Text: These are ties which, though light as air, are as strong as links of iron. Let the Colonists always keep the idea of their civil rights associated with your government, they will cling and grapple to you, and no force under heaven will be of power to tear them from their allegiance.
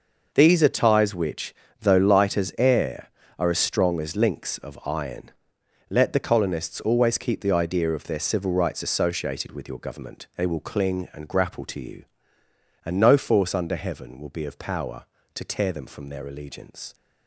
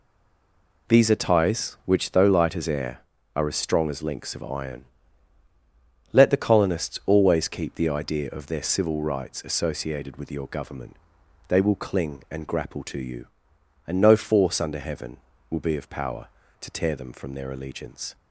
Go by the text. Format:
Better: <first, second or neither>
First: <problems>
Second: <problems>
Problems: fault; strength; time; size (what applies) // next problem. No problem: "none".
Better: first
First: none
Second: stays silent before the first word; slight; until 0.8 s; 0.8 s long